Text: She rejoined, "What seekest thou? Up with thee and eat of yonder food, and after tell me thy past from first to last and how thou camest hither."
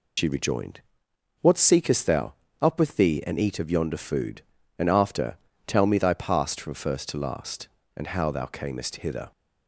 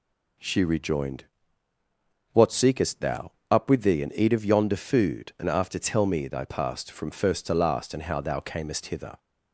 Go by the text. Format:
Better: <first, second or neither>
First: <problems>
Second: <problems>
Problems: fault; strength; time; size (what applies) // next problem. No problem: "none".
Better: second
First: loses the start of "She"; at 0.1 s; 80 ms // pauses between "after" and "tell"; slight; at 5.3 s; 0.32 s long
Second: none